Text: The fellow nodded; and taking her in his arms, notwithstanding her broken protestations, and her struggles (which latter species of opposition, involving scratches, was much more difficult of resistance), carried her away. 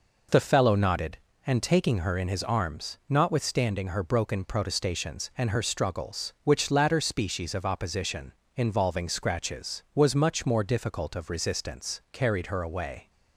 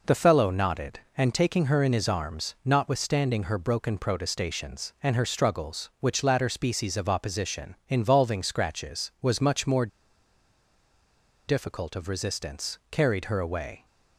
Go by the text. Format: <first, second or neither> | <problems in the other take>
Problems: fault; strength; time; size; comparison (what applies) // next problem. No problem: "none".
first | pauses between "more" and "difficult"; strong; at 9.8 s; 1.6 s long